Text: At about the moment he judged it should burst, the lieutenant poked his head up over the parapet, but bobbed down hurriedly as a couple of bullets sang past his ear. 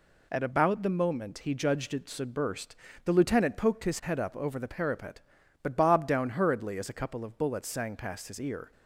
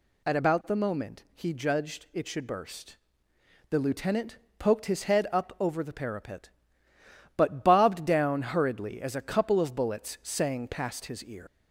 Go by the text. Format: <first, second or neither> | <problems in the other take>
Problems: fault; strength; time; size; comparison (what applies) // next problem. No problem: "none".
first | pauses between "lieutenant" and "poked"; slight; at 4.3 s; 0.20 s long // leaves "ear" unfinished; at 11.4 s; 135 ms